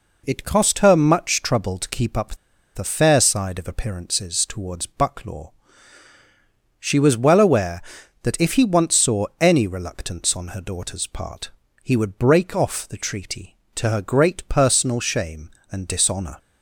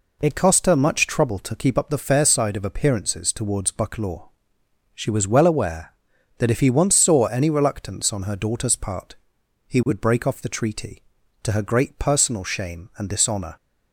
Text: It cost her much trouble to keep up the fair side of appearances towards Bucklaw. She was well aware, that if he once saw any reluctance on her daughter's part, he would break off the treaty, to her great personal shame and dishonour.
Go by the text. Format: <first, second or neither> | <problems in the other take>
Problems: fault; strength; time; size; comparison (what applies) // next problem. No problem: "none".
second | pauses between "up" and "the"; at 2.3 s; 0.38 s long